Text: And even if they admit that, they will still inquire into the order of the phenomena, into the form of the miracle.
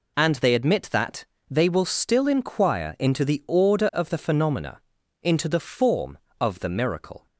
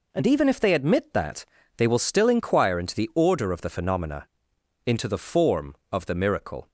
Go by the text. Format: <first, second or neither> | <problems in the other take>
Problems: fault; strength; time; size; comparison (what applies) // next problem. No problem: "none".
second | skips "even if"; at 0.3 s